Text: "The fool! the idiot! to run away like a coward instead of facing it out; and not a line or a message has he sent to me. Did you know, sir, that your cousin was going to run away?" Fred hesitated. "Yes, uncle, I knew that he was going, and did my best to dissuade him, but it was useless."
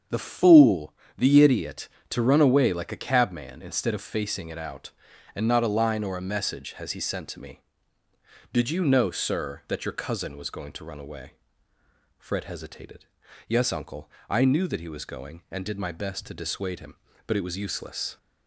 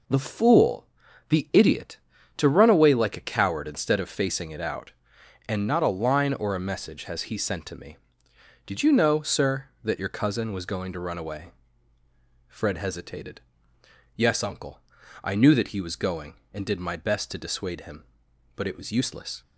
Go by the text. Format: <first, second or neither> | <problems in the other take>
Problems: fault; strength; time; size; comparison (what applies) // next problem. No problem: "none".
second | starts louder than the rest; strong; until 1.3 s; 7.5 dB // says "cabman" for "coward"; at 3.0 s